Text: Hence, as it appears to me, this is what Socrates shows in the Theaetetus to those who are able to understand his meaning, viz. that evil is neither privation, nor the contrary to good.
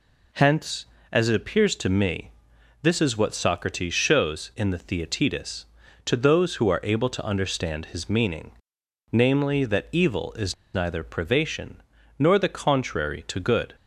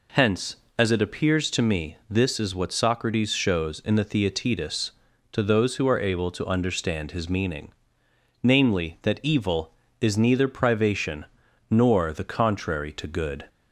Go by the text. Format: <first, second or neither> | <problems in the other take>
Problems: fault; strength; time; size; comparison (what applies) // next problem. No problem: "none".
second | pauses between "is" and "neither"; slight; at 10.5 s; 0.20 s long